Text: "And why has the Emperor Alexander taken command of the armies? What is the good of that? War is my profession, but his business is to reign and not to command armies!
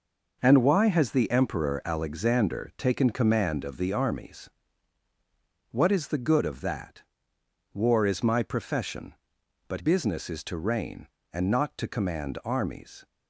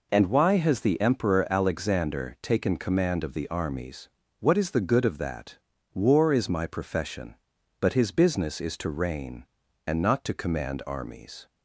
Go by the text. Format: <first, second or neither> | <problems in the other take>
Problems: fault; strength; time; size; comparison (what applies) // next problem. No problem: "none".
second | skips "his"; at 9.7 s